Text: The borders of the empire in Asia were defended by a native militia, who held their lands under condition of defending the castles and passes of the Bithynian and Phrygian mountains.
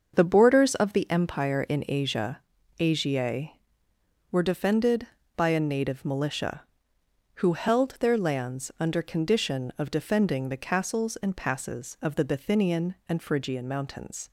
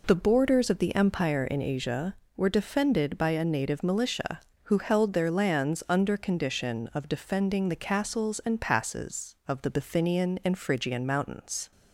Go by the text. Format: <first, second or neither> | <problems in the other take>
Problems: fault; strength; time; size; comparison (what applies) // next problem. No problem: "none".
second | starts louder than the rest; until 1.1 s; 6.5 dB // says "Asia" twice; at 2.7 s